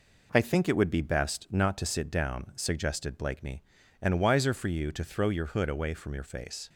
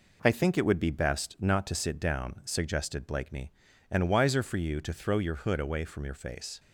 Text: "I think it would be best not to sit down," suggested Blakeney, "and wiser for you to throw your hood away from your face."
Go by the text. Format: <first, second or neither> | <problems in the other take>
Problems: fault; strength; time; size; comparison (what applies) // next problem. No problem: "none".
neither | none